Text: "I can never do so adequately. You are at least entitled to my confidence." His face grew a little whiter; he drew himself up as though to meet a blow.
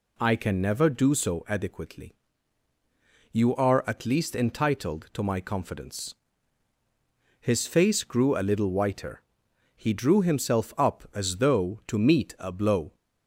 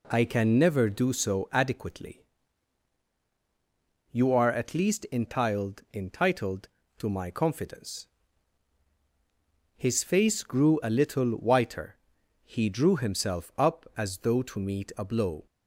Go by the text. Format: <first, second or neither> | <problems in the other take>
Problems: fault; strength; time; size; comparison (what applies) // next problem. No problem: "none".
first | says "entitled" twice; at 5.9 s